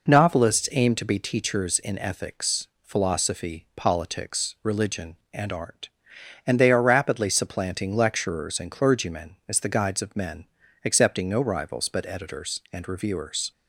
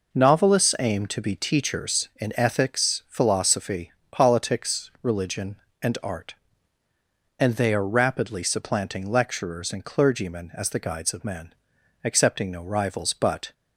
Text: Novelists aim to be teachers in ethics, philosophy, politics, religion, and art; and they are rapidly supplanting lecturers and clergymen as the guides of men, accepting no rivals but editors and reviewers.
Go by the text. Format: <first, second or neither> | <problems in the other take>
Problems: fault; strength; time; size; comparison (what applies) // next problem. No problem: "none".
first | stops before "editors and reviewers"; at 13.5 s